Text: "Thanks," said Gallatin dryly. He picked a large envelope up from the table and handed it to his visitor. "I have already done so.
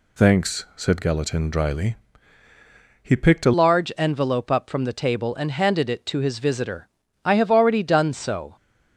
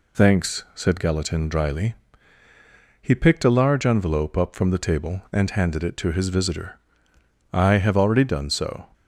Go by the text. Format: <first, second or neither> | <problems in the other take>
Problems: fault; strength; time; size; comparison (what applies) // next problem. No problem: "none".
second | changes voice at "large"; from 3.5 s on; 5.0 s long